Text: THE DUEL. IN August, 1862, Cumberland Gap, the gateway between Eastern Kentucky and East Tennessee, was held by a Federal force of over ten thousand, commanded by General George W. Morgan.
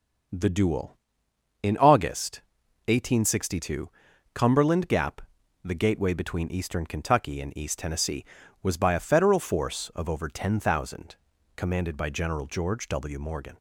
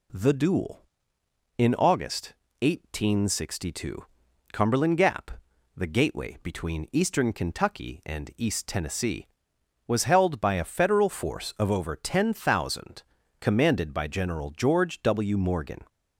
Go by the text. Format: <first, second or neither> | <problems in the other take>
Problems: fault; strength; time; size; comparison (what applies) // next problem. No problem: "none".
second | skips "held"; at 8.7 s